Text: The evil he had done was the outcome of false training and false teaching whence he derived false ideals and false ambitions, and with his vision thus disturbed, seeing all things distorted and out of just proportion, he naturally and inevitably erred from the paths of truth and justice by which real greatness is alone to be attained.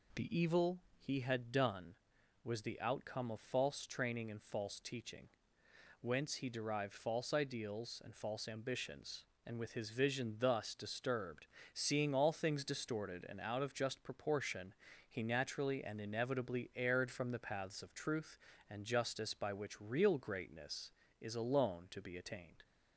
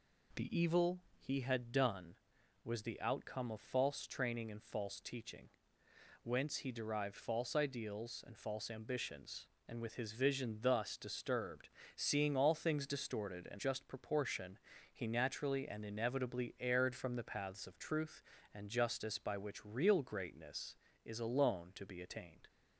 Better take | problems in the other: first | pauses between "evil" and "he"; slight; at 0.9 s; 0.18 s long; slight in the first // pauses between "teaching" and "whence"; noticeable; at 5.4 s; 0.74 s long; noticeable in the first // skips "out of"; at 13.5 s

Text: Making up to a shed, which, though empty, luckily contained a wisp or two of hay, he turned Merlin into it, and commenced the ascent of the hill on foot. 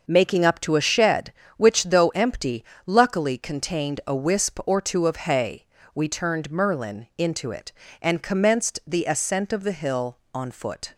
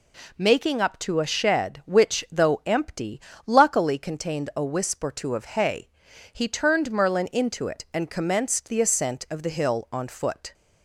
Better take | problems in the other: second | says "we" for "he"; at 5.9 s

